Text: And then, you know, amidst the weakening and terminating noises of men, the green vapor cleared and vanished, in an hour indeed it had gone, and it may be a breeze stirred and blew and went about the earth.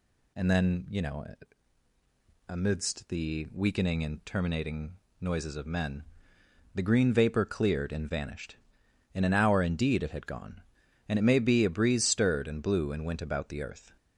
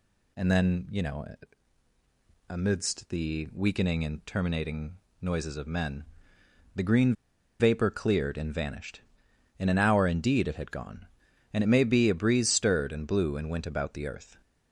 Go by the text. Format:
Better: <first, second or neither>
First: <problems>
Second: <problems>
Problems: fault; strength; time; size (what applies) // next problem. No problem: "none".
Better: first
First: pauses between "terminating" and "noises"; slight; at 4.9 s; 0.26 s long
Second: pauses between "terminating" and "noises"; slight; at 4.9 s; 0.26 s long // pauses between "green" and "vapor"; at 7.1 s; 0.45 s long